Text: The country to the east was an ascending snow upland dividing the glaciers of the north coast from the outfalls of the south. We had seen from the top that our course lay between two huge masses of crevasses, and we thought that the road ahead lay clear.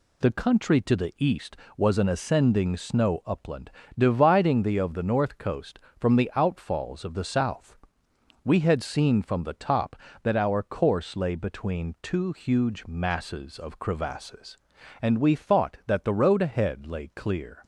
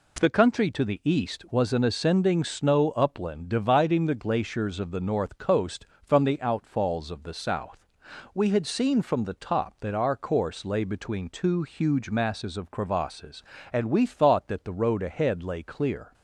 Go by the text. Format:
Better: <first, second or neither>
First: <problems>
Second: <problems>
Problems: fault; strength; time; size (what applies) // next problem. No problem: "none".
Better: second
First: pauses between "upland" and "dividing"; slight; at 3.7 s; 0.26 s long // skips "glaciers"; at 4.7 s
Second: none